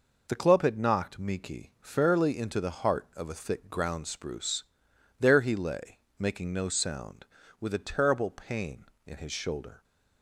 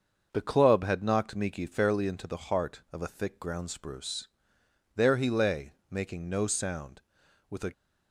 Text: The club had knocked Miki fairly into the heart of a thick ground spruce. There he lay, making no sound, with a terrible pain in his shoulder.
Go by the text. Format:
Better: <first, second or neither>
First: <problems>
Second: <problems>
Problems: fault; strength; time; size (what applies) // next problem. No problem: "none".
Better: first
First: none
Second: starts louder than the rest; until 1.3 s; 6.5 dB // stops before "terrible pain in his shoulder"; at 7.7 s